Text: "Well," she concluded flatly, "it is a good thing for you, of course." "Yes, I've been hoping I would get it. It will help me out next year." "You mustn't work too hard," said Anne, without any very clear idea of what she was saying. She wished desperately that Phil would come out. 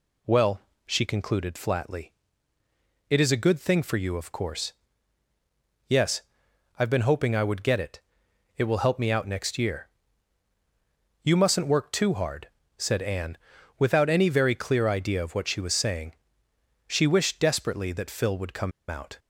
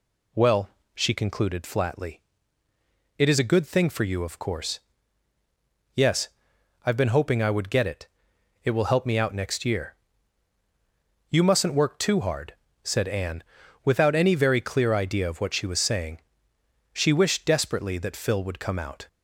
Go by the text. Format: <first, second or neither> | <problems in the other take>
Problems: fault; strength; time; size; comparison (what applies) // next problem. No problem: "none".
second | pauses between "come" and "out"; slight; at 18.7 s; 0.19 s long